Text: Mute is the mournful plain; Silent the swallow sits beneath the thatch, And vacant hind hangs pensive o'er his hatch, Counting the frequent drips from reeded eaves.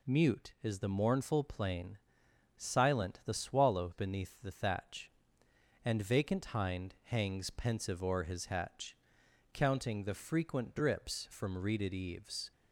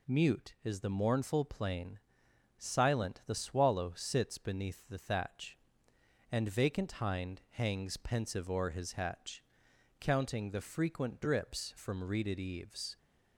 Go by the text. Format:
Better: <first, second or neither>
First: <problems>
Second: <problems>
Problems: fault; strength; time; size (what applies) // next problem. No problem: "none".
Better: second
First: skips "sits"; at 3.9 s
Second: none